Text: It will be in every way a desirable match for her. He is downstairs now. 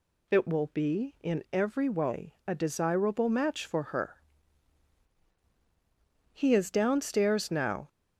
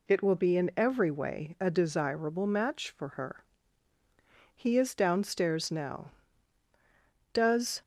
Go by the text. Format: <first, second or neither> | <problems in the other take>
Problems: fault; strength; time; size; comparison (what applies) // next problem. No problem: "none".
first | goes on to say "Does"; slight; from 7.3 s on; 0.48 s long